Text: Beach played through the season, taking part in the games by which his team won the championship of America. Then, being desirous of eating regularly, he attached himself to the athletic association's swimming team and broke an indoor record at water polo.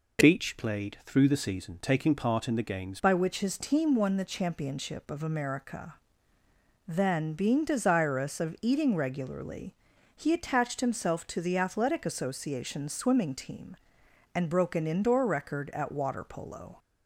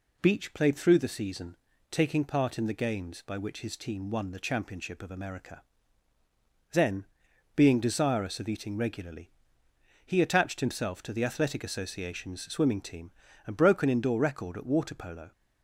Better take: second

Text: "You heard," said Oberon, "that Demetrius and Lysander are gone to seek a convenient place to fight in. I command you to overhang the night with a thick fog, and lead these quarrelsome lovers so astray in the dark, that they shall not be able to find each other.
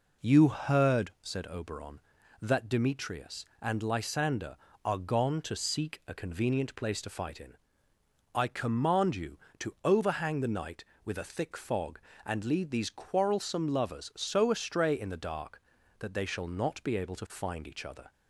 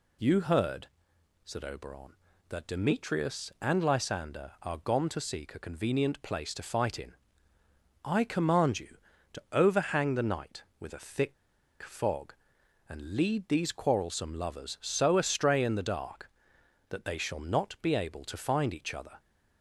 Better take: first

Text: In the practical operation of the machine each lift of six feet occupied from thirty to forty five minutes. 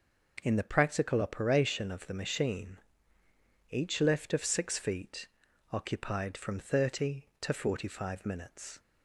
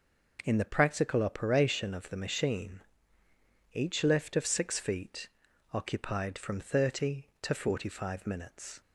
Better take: neither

